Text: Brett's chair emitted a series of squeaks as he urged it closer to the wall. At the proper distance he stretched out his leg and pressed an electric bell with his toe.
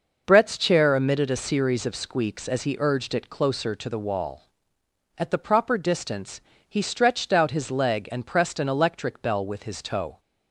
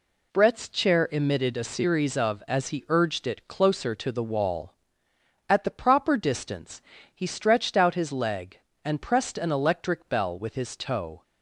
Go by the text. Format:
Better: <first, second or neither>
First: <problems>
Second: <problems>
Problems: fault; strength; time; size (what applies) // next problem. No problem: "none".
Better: first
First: pauses between "distance" and "he"; slight; at 6.3 s; 0.30 s long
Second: skips "squeaks"; at 2.4 s // pauses between "distance" and "he"; slight; at 6.8 s; 0.32 s long